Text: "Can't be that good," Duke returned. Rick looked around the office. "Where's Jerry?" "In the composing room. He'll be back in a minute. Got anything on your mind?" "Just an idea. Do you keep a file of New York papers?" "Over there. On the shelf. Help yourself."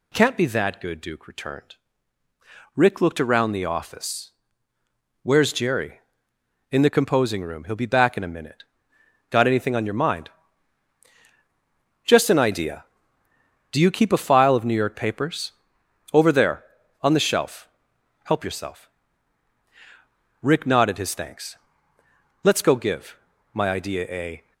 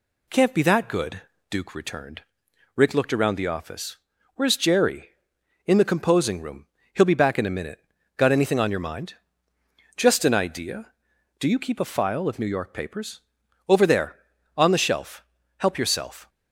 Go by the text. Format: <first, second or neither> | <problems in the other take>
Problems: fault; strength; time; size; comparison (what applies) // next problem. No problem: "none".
second | goes on to say "Rick nodded his thanks Let's go give my idea a"; strong; from 20.4 s on; 4.1 s long